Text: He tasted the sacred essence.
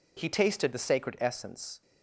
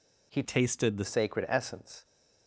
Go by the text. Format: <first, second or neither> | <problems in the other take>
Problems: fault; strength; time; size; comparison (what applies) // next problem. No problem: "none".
first | changes voice from "tasted" to "the"; from 0.4 to 1.0 s; 0.6 s long